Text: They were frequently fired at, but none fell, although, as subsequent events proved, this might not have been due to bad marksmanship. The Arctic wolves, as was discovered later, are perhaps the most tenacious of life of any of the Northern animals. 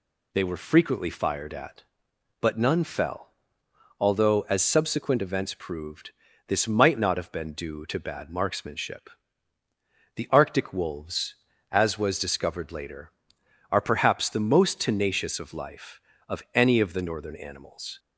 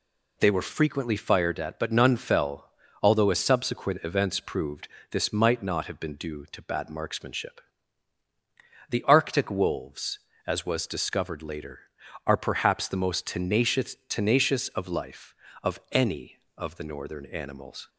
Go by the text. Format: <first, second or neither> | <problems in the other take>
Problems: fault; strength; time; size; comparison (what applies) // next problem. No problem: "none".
first | says "tenacious" twice; at 14.0 s